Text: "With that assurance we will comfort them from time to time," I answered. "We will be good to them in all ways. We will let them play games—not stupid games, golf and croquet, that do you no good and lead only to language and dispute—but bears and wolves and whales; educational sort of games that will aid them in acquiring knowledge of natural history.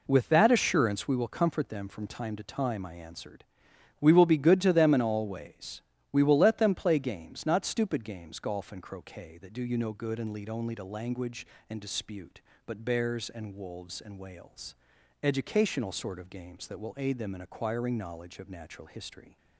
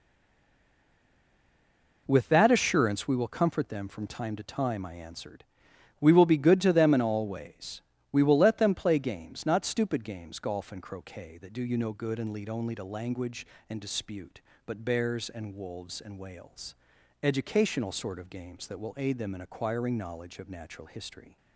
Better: first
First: none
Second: stays silent before the first word; noticeable; until 2.0 s; 2.0 s long

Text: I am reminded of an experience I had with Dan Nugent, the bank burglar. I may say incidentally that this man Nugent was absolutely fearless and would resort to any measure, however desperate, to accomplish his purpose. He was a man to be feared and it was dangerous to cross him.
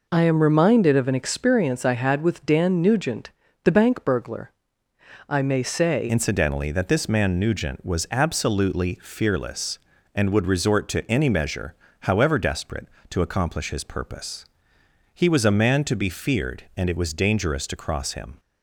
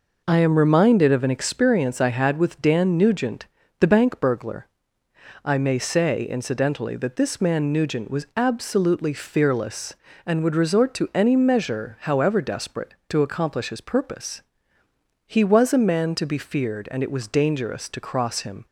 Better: second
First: changes voice at "incidentally"; from 6.0 s on; 12.3 s long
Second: none

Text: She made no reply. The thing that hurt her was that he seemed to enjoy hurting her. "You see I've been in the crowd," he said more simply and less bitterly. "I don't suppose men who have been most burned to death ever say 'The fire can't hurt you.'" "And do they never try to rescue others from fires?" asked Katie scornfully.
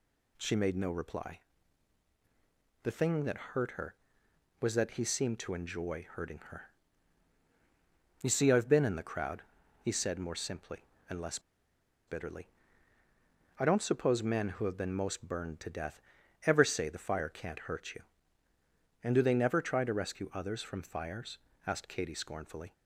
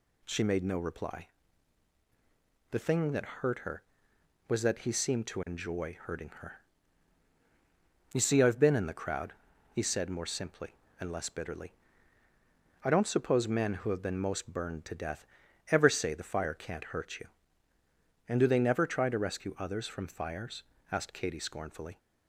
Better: second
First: pauses between "less" and "bitterly"; noticeable; at 11.3 s; 0.68 s long // pauses between "death" and "ever"; at 16.0 s; 0.44 s long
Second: pauses between "death" and "ever"; at 15.2 s; 0.44 s long

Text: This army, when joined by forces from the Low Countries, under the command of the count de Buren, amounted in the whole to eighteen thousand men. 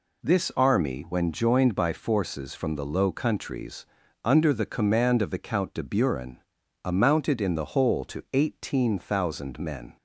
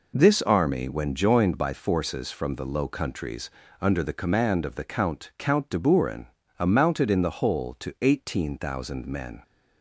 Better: first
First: none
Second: says "count" twice; at 5.3 s

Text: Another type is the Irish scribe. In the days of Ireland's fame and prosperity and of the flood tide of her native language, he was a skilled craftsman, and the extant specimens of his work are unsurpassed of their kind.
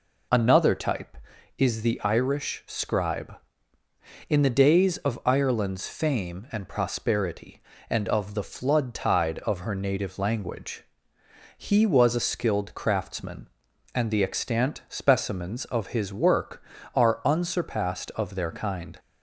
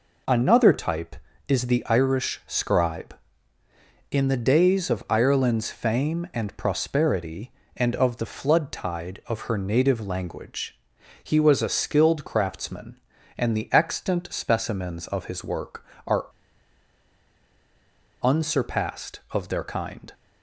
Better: first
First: none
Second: pauses between "are" and "unsurpassed"; strong; at 16.2 s; 1.9 s long

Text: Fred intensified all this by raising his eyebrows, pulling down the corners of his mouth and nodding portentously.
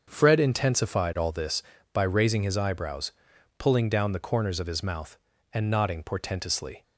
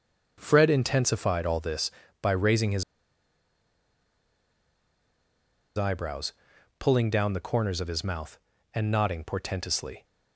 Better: first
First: starts louder than the rest; until 1.0 s; 6.5 dB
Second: starts louder than the rest; until 1.3 s; 6.5 dB // pauses between "his" and "eyebrows"; strong; at 2.8 s; 2.9 s long

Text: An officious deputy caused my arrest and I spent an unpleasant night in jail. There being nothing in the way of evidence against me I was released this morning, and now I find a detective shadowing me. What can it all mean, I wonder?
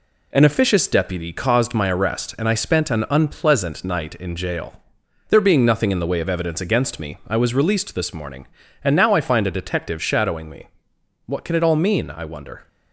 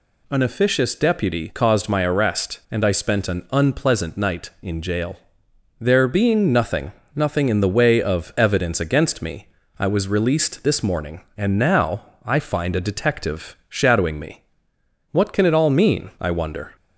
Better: first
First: none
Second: says "nothing" twice; at 7.1 s // pauses between "me" and "I"; slight; at 9.4 s; 0.32 s long // pauses between "now" and "I"; slight; at 12.0 s; 0.18 s long

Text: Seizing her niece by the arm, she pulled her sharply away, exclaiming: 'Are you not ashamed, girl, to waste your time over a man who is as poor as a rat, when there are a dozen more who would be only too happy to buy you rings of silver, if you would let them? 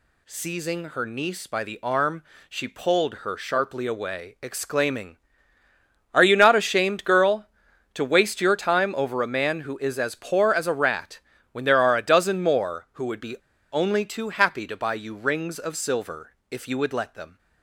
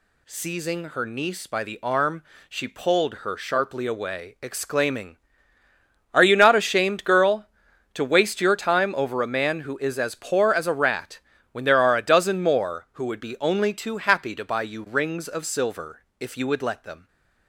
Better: second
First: pauses between "be" and "only"; slight; at 13.3 s; 0.36 s long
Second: none

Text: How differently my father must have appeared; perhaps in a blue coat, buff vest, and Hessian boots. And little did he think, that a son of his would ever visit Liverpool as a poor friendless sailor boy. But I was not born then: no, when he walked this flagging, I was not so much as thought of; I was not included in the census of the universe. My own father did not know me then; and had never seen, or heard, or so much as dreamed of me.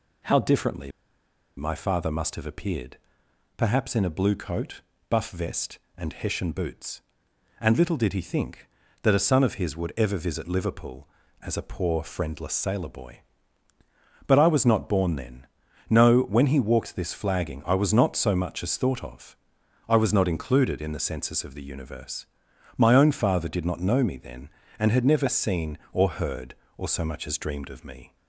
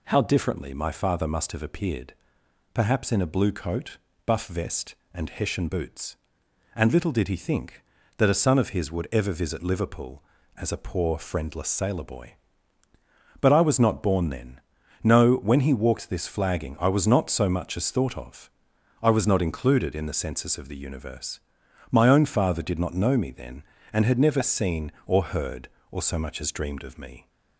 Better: second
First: pauses between "differently" and "my"; noticeable; at 0.8 s; 0.67 s long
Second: none

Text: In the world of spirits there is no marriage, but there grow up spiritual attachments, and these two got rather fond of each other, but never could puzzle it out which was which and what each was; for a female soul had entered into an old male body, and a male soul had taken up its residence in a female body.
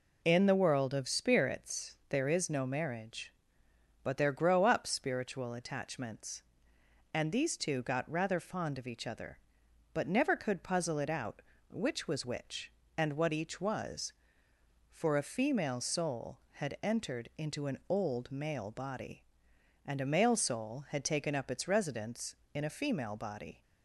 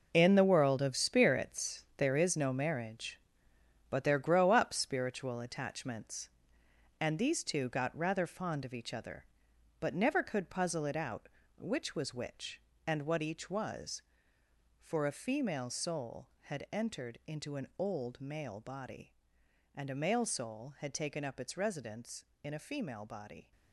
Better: first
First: none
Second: gets quieter; strong; throughout; 10.5 dB

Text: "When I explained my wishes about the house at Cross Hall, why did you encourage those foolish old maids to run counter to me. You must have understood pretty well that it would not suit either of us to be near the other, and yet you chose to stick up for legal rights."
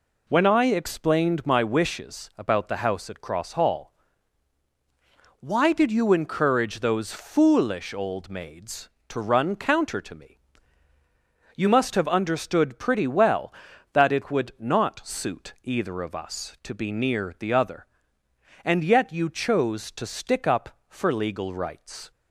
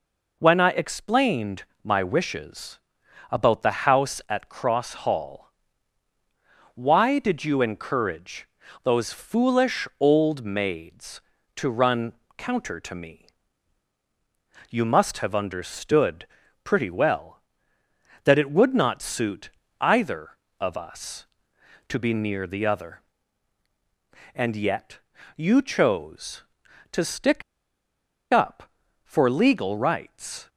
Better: first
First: none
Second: pauses between "explained" and "my"; slight; at 1.6 s; 0.20 s long // pauses between "wishes" and "about"; noticeable; at 2.7 s; 0.50 s long // pauses between "encourage" and "those"; slight; at 8.4 s; 0.34 s long // pauses between "run" and "counter"; slight; at 12.1 s; 0.22 s long // pauses between "understood" and "pretty"; at 16.2 s; 0.38 s long // pauses between "suit" and "either"; slight; at 19.4 s; 0.30 s long // pauses between "yet" and "you"; at 24.9 s; 0.38 s long // pauses between "stick" and "up"; noticeable; at 27.4 s; 0.89 s long

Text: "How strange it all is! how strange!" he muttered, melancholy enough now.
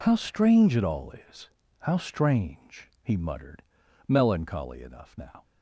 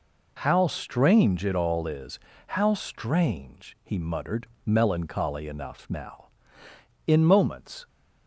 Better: first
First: none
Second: goes on to say "In moments"; noticeable; from 7.0 s on; 0.80 s long

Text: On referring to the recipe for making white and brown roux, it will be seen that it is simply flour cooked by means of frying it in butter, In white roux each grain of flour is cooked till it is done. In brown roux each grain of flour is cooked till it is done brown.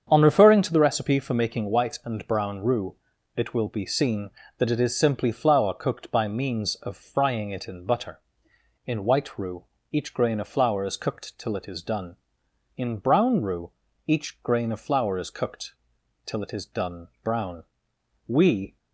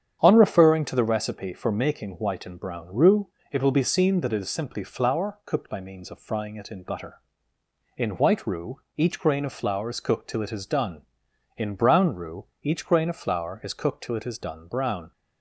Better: second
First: starts louder than the rest; strong; until 1.1 s; 7.5 dB // pauses between "roux" and "each"; slight; at 9.6 s; 0.26 s long // pauses between "roux" and "each"; slight; at 13.7 s; 0.36 s long // pauses between "cooked" and "till"; noticeable; at 15.7 s; 0.50 s long // goes on to say "We"; from 18.2 s on; 0.52 s long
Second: starts louder than the rest; strong; until 1.2 s; 8.5 dB // pauses between "roux" and "each"; slight; at 8.8 s; 0.16 s long // pauses between "roux" and "each"; slight; at 12.4 s; 0.18 s long

